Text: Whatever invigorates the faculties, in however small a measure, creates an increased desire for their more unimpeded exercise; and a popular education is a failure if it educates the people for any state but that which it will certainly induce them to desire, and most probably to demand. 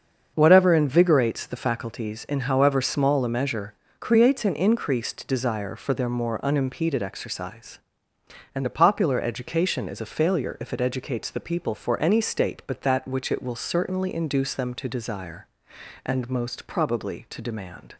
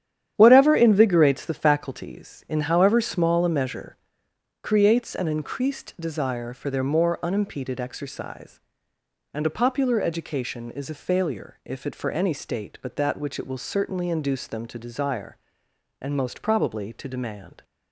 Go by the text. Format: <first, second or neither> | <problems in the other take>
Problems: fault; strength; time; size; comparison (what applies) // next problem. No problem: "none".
first | starts louder than the rest; strong; until 1.3 s; 10 dB; also in the first // skips "educates the people"; at 11.9 s